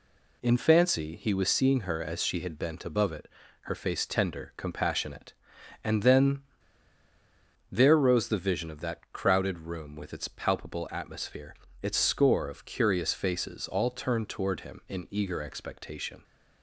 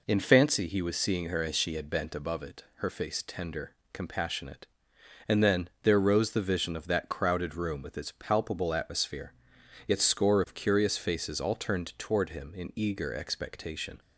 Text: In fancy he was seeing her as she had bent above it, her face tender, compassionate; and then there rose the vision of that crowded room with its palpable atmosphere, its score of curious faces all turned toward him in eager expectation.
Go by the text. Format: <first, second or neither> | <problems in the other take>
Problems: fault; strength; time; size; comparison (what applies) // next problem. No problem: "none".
second | pauses between "then" and "there"; strong; at 6.4 s; 1.2 s long